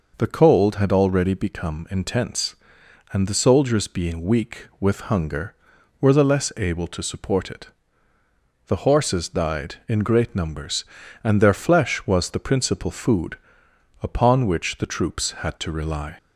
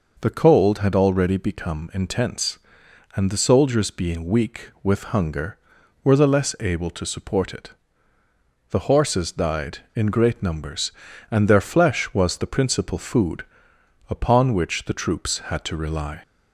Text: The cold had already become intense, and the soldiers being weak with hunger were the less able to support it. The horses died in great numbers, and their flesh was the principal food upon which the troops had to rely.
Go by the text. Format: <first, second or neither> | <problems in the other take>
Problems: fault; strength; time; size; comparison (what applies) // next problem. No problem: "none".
neither | pauses between "food" and "upon"; noticeable; the same in both